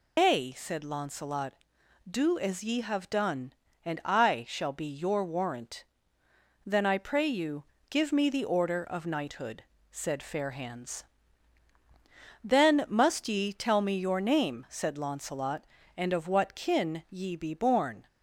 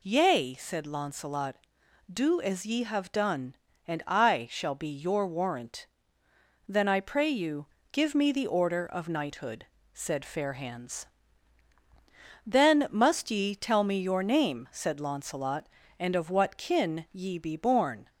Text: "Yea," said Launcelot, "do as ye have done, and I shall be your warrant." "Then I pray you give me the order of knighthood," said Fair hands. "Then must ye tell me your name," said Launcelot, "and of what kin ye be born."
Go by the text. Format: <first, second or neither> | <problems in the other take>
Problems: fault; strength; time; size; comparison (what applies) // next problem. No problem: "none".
second | loses the start of "Yea"; at 0.1 s; 155 ms // pauses between "you" and "give"; slight; at 7.6 s; 0.24 s long; slight in the second